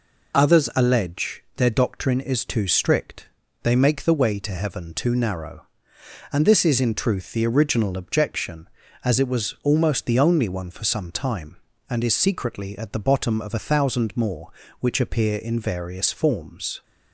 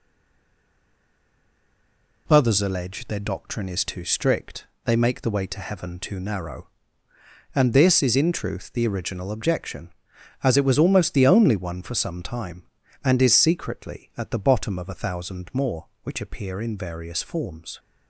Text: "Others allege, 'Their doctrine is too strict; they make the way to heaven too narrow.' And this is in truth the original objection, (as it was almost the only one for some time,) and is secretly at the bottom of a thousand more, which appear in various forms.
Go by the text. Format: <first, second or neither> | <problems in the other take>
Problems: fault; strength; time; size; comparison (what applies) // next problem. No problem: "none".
first | stays silent before the first word; until 2.2 s; 2.2 s long